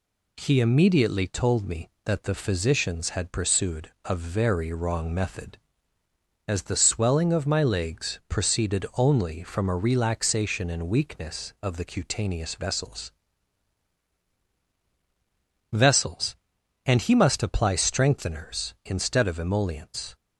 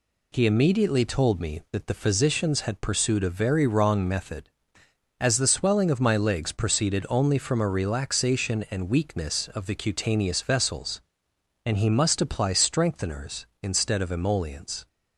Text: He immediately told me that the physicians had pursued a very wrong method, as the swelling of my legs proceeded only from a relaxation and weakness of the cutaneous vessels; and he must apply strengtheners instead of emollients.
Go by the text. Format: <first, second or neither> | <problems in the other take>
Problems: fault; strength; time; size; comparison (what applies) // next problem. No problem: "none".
second | says "vessels" twice; at 15.7 s